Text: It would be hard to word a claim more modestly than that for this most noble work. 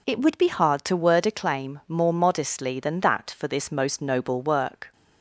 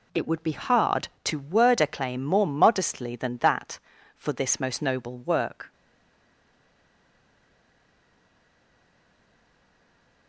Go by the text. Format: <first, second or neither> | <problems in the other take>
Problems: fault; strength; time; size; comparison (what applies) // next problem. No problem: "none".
first | stays silent after the last word; strong; from 5.7 s on; 4.5 s long